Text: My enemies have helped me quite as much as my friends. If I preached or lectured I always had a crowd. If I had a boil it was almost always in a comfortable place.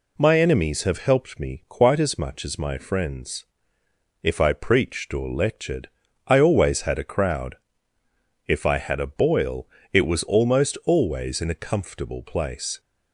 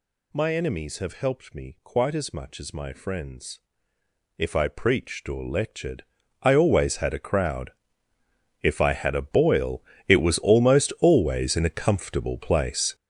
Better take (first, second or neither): first